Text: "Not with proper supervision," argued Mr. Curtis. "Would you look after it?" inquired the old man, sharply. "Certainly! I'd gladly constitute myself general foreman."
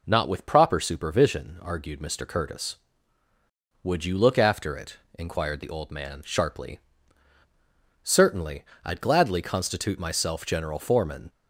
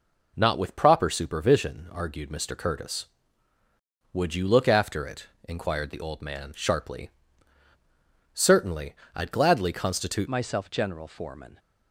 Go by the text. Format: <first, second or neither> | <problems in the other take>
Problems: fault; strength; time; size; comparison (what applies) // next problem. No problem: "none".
first | changes voice at "myself"; from 10.2 s on; 1.3 s long